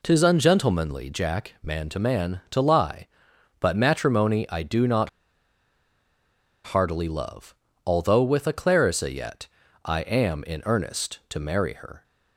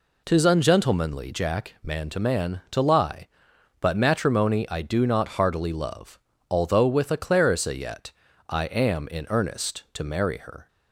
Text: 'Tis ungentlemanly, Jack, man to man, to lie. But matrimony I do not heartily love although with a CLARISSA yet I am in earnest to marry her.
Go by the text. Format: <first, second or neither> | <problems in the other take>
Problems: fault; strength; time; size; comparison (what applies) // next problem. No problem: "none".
second | pauses between "not" and "heartily"; strong; at 5.0 s; 1.5 s long // pauses between "love" and "although"; slight; at 7.5 s; 0.34 s long; slight in the second // pauses between "yet" and "I"; at 9.4 s; 0.38 s long; also in the second